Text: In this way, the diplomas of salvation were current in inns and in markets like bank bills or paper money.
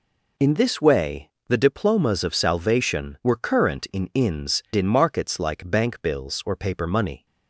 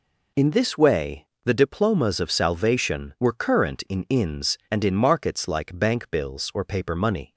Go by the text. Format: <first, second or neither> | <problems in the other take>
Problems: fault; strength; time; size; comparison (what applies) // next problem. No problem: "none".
second | skips "and"; at 4.6 s